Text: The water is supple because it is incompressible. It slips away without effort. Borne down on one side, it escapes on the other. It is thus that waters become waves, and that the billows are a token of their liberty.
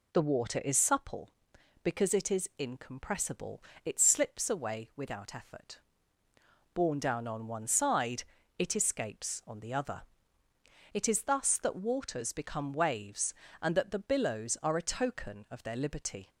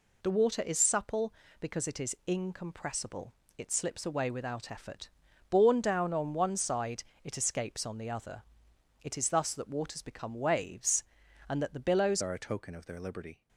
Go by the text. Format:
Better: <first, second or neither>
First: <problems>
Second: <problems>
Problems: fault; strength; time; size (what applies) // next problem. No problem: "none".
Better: first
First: none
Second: changes voice at "are"; from 12.2 s on; 1.2 s long